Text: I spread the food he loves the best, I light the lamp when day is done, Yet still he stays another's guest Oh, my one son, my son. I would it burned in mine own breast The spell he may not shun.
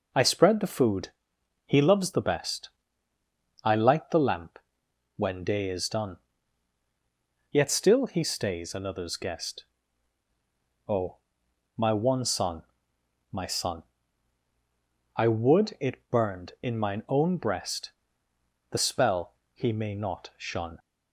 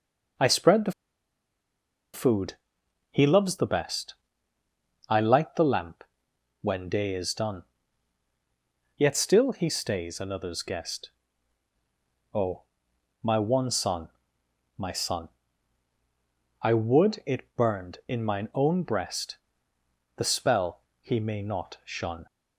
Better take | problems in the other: first | pauses between "the" and "food"; at 0.9 s; 1.2 s long // pauses between "food" and "he"; noticeable; at 2.5 s; 0.56 s long; noticeable in the first // pauses between "lamp" and "when"; noticeable; at 6.0 s; 0.56 s long; noticeable in the first // pauses between "guest" and "Oh"; at 11.1 s; 1.2 s long; also in the first // pauses between "breast" and "The"; noticeable; at 19.3 s; 0.80 s long; noticeable in the first // pauses between "spell" and "he"; slight; at 20.8 s; 0.20 s long; slight in the first

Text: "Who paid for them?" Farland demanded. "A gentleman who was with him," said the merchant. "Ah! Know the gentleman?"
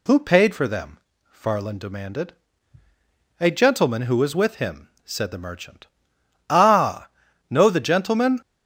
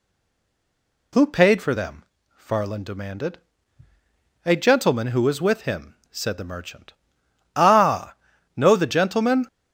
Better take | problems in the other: first | stays silent before the first word; until 1.1 s; 1.1 s long

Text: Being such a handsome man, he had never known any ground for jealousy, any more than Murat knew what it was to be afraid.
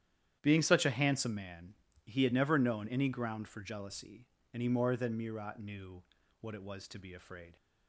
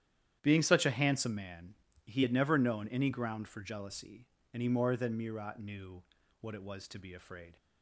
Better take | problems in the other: neither | starts louder than the rest; strong; the same in both // pauses between "knew" and "what"; the same in both

